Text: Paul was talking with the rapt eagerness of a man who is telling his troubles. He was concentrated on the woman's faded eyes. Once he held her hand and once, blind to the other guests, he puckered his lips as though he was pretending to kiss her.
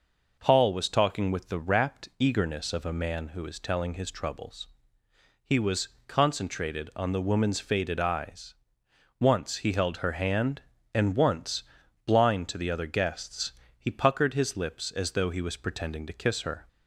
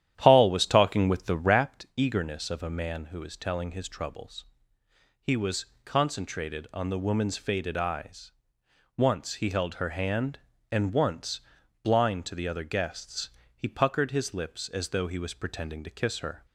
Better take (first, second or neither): first